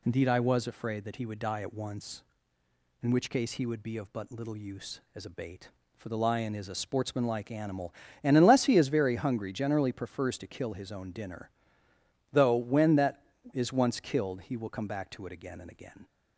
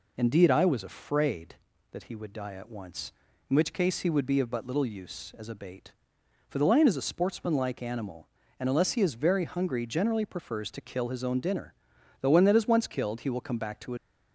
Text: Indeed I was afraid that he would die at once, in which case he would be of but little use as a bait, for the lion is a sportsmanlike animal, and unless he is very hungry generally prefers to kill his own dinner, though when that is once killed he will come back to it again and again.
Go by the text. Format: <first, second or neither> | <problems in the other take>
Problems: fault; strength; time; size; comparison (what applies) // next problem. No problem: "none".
first | stops before "again and again"; at 13.9 s